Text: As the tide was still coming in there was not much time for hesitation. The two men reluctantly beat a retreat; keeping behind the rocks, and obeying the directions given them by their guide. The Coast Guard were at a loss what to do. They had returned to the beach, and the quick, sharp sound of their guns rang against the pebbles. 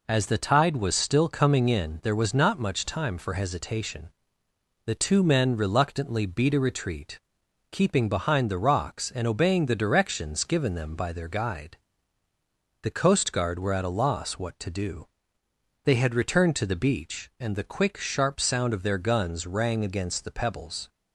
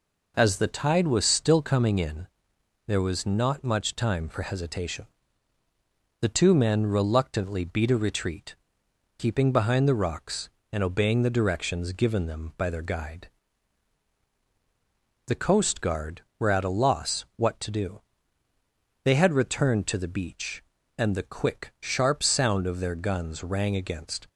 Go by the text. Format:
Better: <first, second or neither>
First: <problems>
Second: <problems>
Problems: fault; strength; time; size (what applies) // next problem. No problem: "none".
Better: first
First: none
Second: pauses between "in" and "there"; noticeable; at 2.2 s; 0.60 s long // stops before "the pebbles"; at 24.2 s